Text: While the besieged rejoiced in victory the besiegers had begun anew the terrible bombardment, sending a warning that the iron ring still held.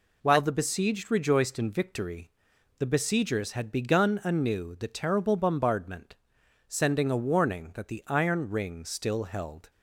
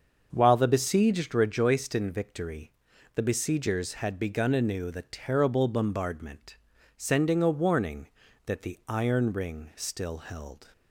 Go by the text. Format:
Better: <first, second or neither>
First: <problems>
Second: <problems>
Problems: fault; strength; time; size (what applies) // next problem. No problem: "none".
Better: first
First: pauses between "victory" and "the"; noticeable; at 2.3 s; 0.50 s long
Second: starts louder than the rest; until 1.5 s; 6.5 dB // pauses between "victory" and "the"; at 2.7 s; 0.44 s long